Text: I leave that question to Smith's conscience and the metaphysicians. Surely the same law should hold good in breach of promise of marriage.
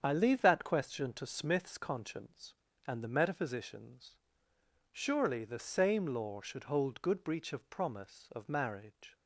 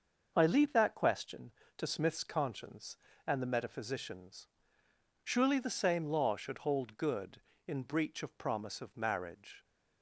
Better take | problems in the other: second | starts louder than the rest; strong; until 1.0 s; 8 dB; also in the second // skips "in"; at 7.2 s

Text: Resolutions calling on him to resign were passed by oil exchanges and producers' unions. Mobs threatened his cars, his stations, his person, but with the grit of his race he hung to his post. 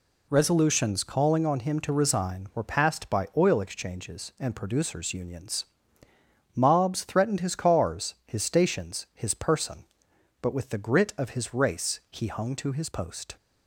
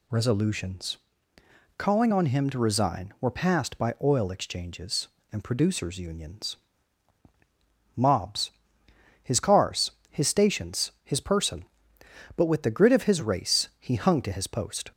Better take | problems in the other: first | pauses between "Resolutions" and "calling"; noticeable; at 0.9 s; 0.80 s long // skips "threatened"; at 8.8 s

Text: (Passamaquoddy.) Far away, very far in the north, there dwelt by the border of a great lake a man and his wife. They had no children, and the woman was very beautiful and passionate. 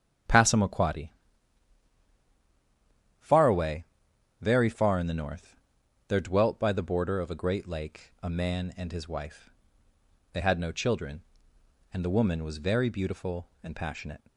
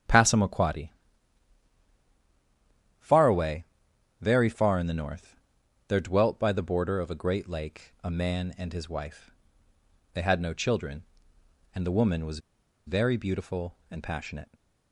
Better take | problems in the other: first | starts louder than the rest; strong; until 3.1 s; 9 dB; strong in the first // pauses between "was" and "very"; noticeable; at 12.3 s; 0.48 s long

